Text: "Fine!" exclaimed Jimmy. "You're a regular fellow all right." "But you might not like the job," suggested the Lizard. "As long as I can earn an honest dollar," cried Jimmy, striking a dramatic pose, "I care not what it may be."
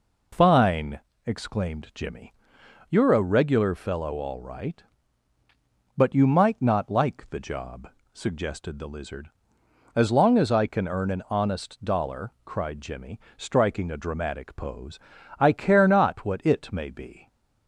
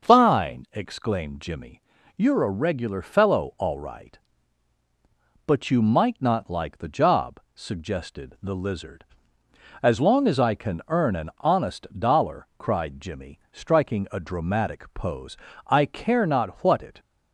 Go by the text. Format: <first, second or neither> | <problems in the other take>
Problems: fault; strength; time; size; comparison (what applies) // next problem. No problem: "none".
first | starts louder than the rest; until 1.1 s; 6 dB // stops before "may be"; at 16.9 s